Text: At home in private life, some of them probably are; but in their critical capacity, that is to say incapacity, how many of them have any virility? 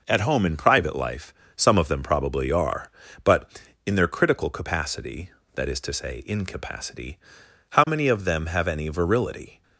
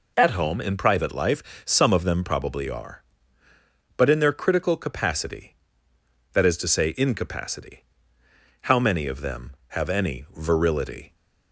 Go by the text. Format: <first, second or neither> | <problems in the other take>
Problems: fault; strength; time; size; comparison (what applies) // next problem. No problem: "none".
neither | none